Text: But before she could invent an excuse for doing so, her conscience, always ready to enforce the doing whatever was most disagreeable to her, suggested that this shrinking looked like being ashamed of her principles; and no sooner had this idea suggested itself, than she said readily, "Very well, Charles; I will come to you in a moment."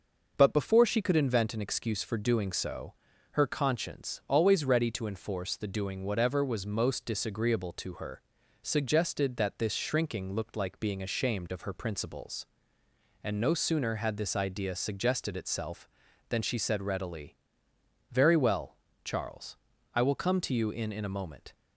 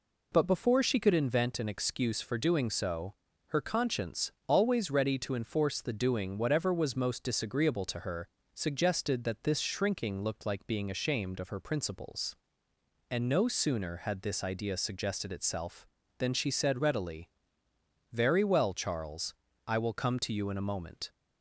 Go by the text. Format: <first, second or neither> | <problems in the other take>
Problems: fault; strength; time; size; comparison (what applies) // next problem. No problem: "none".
second | says "in" twice; at 20.9 s